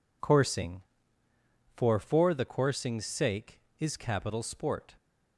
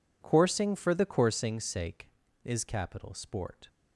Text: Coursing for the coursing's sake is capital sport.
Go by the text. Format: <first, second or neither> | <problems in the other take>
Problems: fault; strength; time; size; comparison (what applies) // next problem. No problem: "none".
second | says "for" twice; at 1.9 s